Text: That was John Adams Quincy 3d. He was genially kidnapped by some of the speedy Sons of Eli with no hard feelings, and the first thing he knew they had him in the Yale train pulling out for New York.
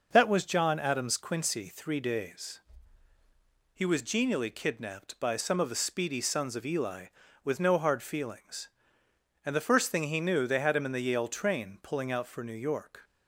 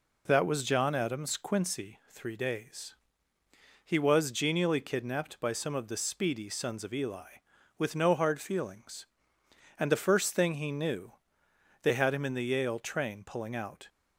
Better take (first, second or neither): first